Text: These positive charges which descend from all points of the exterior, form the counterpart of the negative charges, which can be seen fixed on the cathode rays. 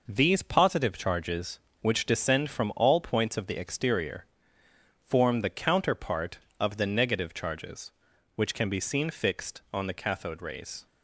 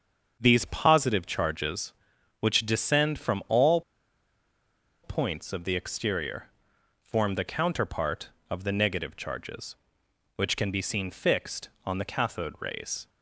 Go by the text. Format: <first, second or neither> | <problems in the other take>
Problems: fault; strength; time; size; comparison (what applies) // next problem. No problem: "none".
first | starts louder than the rest; until 1.4 s; 7 dB // pauses between "all" and "points"; at 3.8 s; 1.2 s long